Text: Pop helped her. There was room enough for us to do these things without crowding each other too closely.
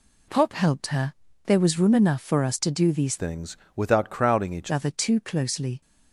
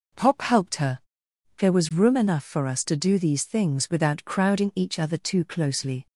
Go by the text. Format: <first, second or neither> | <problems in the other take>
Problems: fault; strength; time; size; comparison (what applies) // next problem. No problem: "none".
second | changes voice from "things" to "each"; from 3.1 to 4.7 s; 1.6 s long // pauses between "things" and "without"; slight; at 3.5 s; 0.20 s long